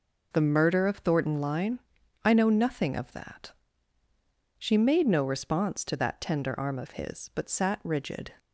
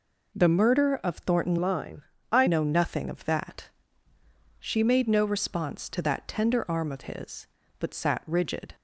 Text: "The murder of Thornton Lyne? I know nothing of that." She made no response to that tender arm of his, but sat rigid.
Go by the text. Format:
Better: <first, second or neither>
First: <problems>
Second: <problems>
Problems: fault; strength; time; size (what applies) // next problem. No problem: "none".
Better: first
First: none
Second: changes voice from "Lyne" to "I"; from 1.6 to 2.4 s; 0.8 s long